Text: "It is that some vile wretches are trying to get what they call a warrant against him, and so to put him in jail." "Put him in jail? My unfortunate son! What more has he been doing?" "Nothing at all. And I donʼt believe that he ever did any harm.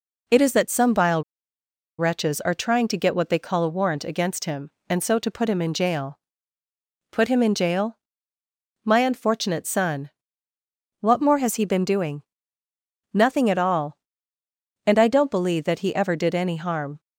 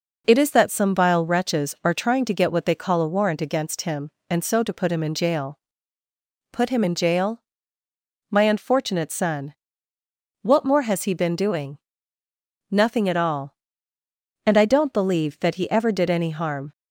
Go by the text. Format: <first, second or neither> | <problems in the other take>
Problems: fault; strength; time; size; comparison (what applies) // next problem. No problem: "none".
second | pauses between "vile" and "wretches"; noticeable; at 1.2 s; 0.75 s long